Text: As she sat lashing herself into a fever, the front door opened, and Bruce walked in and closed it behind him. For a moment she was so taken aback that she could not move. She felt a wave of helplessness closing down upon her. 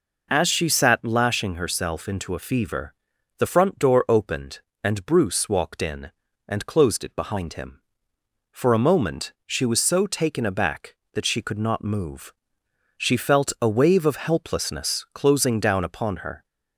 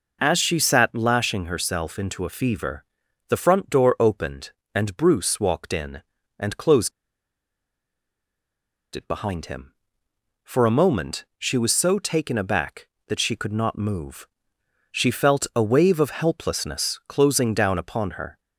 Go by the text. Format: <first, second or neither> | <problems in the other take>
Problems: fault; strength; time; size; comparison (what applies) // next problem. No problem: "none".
first | pauses between "closed" and "it"; strong; at 6.9 s; 2.0 s long